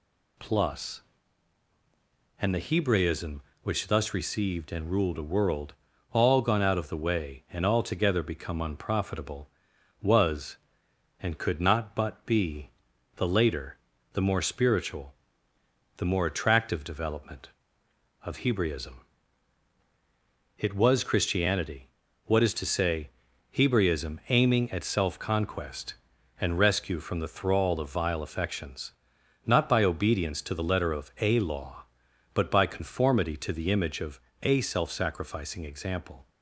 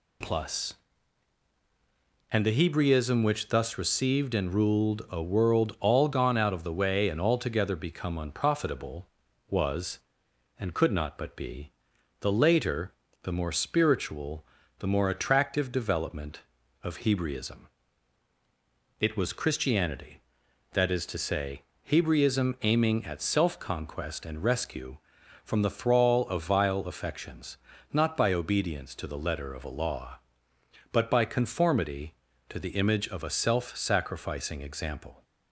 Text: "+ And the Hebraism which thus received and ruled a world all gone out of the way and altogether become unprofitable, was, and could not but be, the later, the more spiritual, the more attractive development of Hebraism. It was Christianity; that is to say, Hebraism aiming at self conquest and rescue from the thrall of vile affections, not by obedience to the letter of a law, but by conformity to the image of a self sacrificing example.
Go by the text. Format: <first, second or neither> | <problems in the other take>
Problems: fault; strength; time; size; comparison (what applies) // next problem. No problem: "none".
second | pauses between "world" and "all"; at 5.7 s; 0.38 s long // says "what" for "that"; at 22.2 s // pauses between "of" and "a"; slight; at 34.2 s; 0.22 s long